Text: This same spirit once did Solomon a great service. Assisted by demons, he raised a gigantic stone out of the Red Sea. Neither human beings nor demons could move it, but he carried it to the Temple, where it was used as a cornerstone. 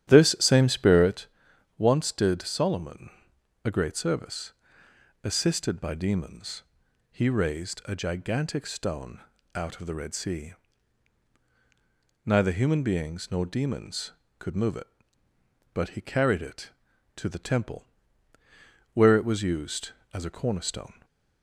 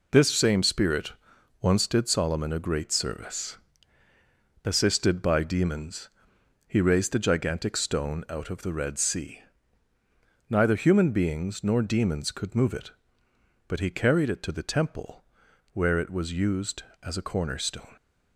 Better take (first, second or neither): second